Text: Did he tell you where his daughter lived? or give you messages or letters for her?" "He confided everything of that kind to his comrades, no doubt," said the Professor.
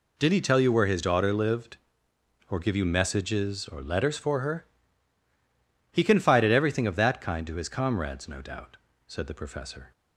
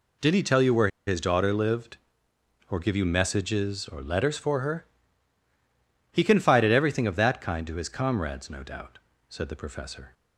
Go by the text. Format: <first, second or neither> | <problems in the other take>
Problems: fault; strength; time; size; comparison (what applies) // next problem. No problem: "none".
first | pauses between "where" and "his"; slight; at 0.8 s; 0.18 s long